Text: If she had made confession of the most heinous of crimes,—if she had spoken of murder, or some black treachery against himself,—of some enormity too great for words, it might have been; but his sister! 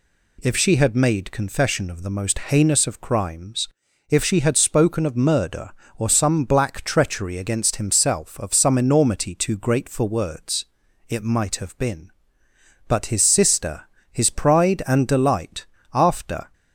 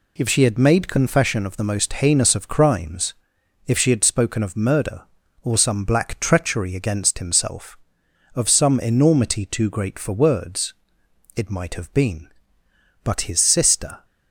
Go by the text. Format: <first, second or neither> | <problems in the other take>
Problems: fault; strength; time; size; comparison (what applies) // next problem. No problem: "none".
second | goes on to say "his pride and delight after"; strong; from 14.1 s on; 2.3 s long